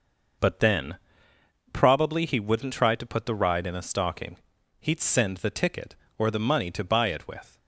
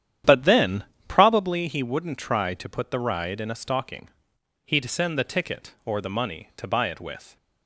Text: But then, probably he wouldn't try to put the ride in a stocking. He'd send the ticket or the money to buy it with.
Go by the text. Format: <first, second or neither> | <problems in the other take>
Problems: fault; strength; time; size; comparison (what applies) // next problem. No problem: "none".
first | starts louder than the rest; strong; until 1.6 s; 10 dB